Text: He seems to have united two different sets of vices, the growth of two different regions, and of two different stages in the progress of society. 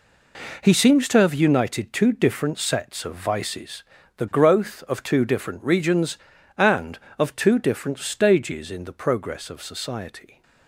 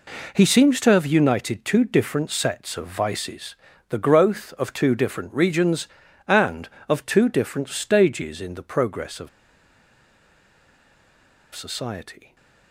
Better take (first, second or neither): first